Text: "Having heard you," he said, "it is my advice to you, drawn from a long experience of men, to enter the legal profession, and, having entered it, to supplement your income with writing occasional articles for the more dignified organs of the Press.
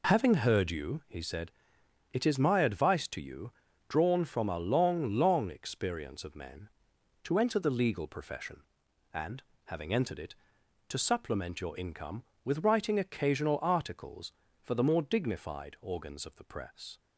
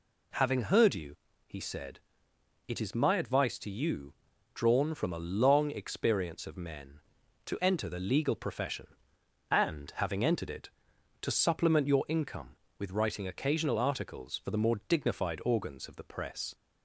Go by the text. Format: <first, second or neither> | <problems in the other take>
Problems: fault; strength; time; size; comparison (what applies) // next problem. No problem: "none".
second | says "long" twice; at 5.1 s